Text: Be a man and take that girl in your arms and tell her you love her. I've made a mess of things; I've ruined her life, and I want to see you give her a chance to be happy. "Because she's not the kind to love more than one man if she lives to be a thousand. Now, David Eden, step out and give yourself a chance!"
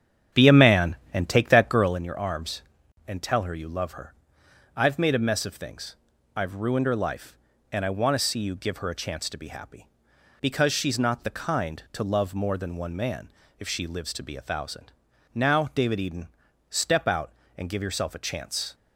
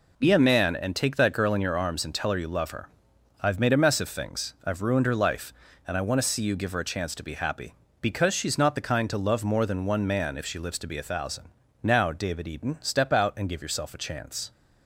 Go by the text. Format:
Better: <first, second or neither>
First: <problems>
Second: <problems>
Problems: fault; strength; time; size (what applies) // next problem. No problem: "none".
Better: second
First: starts louder than the rest; strong; until 2.0 s; 8.5 dB // pauses between "man" and "if"; slight; at 13.3 s; 0.28 s long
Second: none